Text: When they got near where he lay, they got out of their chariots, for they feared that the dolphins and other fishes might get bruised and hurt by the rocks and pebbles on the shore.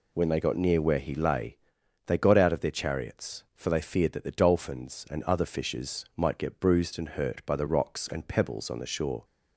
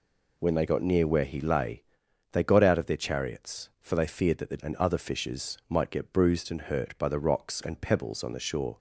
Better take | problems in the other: first | skips "dolphins"; at 4.5 s

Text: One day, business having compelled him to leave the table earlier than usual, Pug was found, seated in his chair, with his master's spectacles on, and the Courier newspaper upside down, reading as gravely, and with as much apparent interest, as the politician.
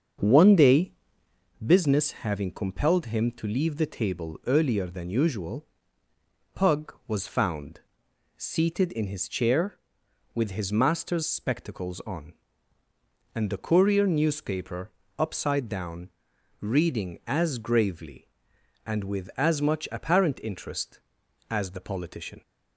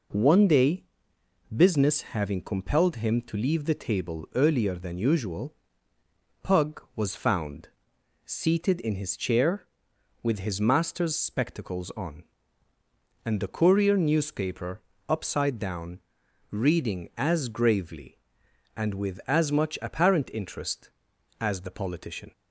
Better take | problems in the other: second | starts louder than the rest; until 1.5 s; 7 dB // pauses between "newspaper" and "upside"; slight; at 14.8 s; 0.30 s long; slight in the second

